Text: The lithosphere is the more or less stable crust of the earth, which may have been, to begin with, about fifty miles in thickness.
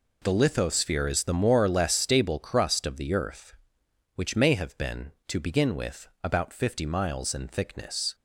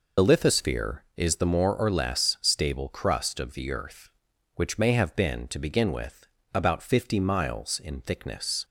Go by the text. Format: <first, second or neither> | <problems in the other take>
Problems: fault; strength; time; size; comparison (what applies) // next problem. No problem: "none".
first | loses the start of "The"; at 0.1 s; 50 ms